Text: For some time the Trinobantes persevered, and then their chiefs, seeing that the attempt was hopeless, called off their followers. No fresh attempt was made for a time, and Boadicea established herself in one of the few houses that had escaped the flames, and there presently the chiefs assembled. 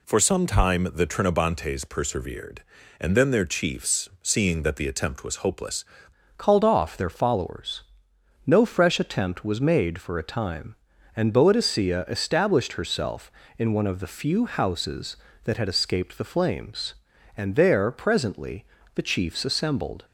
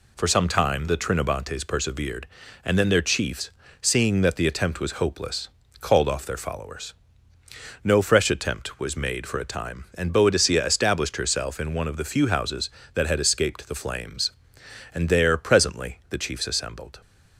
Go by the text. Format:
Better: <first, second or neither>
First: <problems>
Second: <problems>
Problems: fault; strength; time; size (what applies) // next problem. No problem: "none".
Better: second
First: changes voice at "called"; from 6.3 s on; 13.7 s long // pauses between "presently" and "the"; slight; at 18.6 s; 0.28 s long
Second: none